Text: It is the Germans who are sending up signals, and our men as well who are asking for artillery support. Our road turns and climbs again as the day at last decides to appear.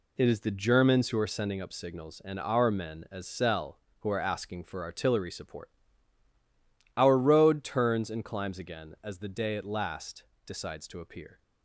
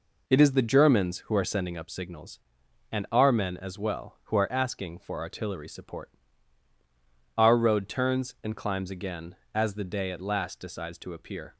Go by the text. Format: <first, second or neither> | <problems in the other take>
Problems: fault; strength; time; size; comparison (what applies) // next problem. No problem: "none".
second | says "cell" for "well"; at 3.2 s // pauses between "last" and "decides"; slight; at 10.2 s; 0.24 s long